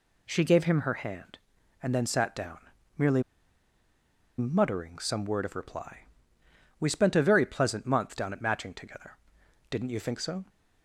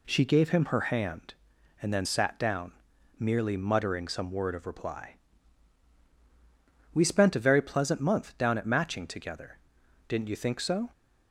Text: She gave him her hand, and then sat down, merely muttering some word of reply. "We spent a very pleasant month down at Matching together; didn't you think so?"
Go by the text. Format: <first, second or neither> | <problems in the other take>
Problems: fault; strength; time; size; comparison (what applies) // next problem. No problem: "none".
second | pauses between "merely" and "muttering"; at 3.2 s; 1.1 s long